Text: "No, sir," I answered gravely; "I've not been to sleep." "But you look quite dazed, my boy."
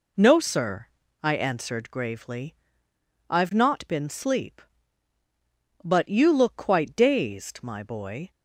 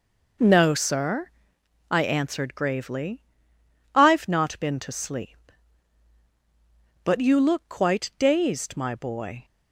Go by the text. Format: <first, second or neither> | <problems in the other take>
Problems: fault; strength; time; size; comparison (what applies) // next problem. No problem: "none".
second | skips "to"; at 4.0 s